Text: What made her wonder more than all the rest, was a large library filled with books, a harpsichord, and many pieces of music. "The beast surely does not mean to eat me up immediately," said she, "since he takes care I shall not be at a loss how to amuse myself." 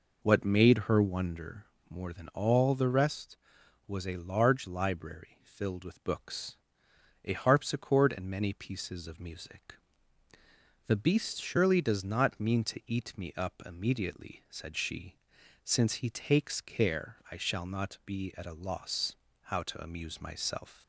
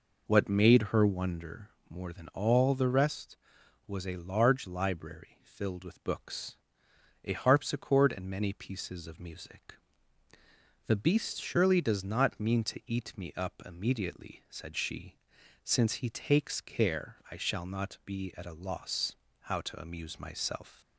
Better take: neither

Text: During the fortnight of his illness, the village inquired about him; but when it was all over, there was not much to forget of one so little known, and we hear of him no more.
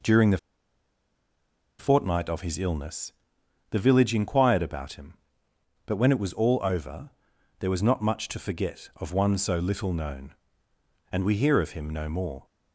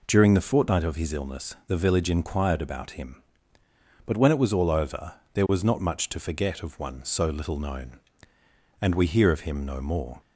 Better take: second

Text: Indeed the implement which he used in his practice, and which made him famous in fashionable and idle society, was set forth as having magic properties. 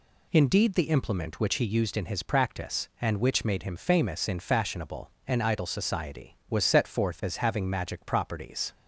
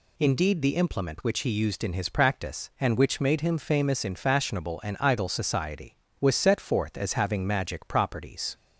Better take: neither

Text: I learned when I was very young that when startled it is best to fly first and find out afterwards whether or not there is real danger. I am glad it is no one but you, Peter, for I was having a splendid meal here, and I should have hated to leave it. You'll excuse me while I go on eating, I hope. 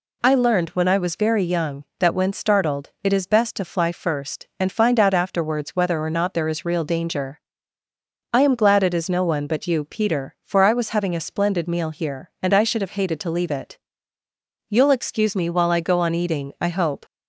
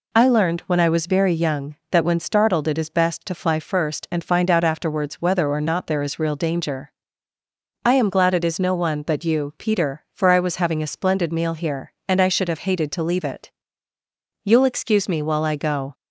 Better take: first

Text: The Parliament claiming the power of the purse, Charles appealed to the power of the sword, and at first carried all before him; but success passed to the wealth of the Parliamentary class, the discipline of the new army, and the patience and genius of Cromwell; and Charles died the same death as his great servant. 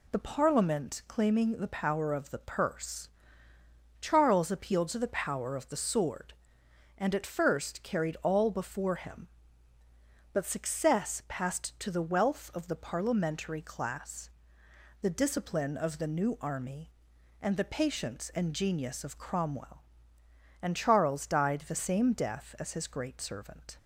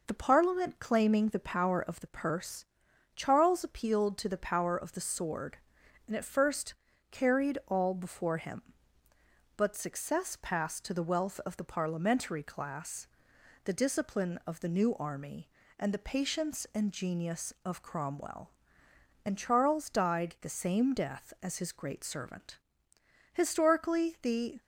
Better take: first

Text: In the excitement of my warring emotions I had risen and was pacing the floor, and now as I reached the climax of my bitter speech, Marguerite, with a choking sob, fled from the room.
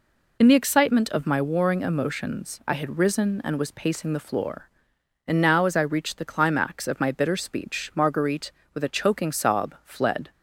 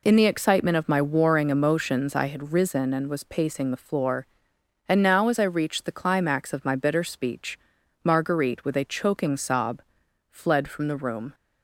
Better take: second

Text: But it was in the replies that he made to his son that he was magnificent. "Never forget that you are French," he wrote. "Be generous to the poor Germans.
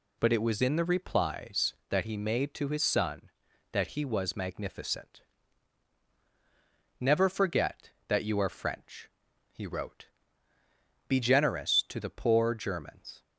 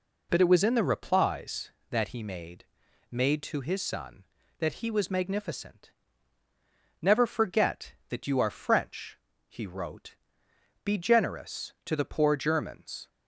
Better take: first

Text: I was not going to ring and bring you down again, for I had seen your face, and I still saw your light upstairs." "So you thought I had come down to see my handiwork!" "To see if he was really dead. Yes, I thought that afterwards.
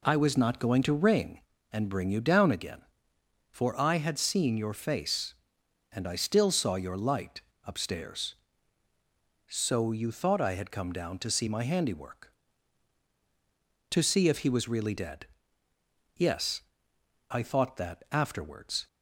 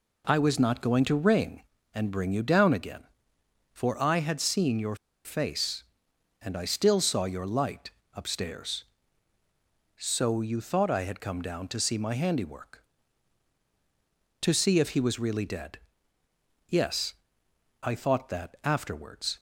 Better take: first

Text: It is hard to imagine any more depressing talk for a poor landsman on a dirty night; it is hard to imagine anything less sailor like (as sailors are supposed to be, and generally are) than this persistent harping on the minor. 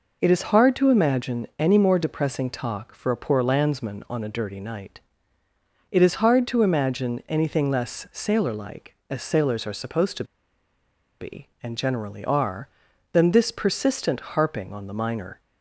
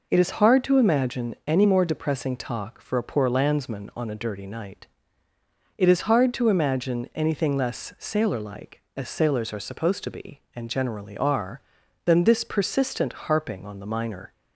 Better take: second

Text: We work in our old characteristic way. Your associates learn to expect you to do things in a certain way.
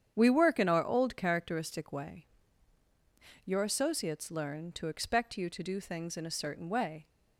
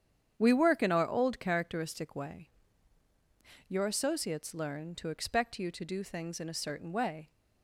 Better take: neither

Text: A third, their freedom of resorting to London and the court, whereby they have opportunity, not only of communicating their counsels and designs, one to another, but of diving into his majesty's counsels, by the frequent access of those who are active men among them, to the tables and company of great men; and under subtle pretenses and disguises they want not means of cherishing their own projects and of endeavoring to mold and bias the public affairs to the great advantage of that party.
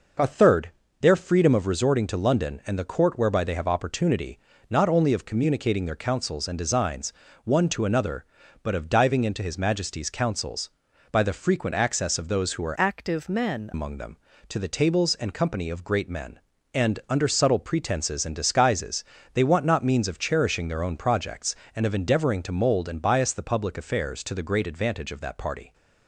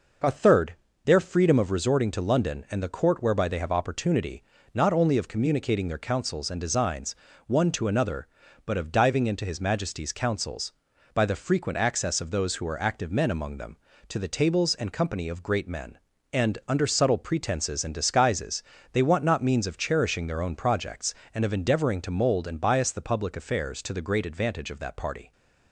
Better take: second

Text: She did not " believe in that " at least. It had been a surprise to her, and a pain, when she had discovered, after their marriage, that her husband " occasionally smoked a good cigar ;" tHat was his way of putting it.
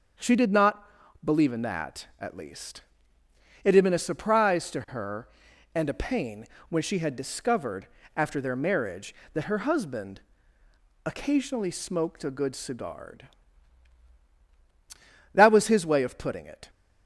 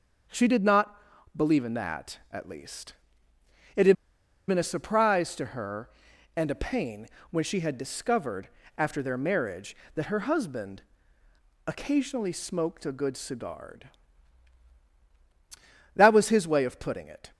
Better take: first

